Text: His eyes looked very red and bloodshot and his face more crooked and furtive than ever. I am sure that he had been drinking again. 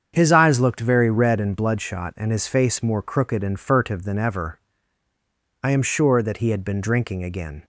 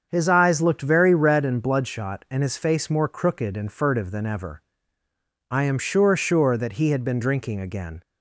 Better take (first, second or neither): first